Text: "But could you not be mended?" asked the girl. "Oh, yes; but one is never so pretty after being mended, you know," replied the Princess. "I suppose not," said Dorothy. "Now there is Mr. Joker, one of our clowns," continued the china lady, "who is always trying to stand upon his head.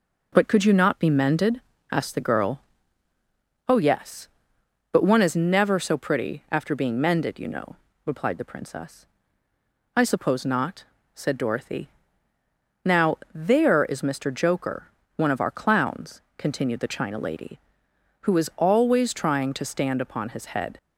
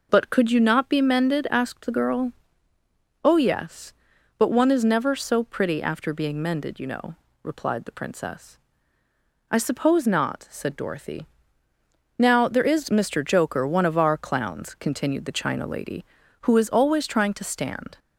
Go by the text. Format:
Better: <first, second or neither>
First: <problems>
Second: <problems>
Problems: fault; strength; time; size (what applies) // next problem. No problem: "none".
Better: first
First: none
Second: stops before "upon his head"; at 17.9 s